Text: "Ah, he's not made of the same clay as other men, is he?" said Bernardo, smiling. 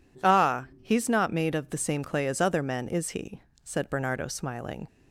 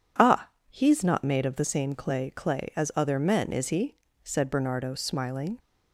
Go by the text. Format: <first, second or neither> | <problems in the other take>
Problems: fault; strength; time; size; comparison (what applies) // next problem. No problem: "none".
first | says "clay" twice; at 2.2 s